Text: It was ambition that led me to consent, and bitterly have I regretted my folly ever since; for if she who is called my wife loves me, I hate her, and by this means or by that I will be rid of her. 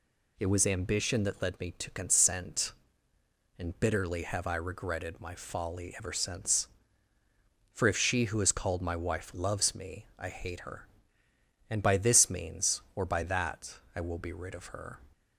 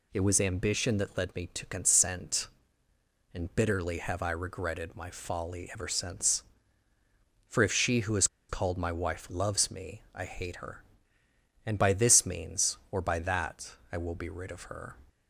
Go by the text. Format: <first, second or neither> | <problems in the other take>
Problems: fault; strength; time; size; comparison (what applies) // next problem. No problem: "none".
first | pauses between "is" and "called"; slight; at 8.2 s; 0.23 s long // pauses between "that" and "I"; slight; at 13.7 s; 0.16 s long; slight in the first